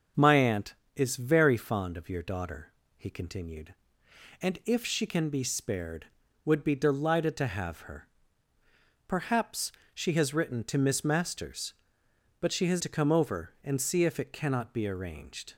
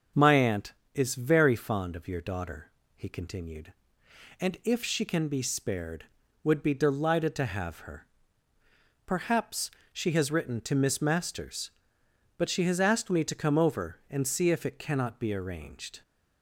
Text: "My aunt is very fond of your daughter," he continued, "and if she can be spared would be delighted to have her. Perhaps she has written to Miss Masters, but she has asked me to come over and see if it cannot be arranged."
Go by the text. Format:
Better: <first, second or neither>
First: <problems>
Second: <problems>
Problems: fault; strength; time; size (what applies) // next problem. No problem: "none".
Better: second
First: starts louder than the rest; until 1.3 s; 6.5 dB // pauses between "Perhaps" and "she"; slight; at 9.7 s; 0.20 s long // skips "asked me"; at 12.7 s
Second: starts louder than the rest; until 1.3 s; 6.5 dB // pauses between "Perhaps" and "she"; slight; at 9.7 s; 0.20 s long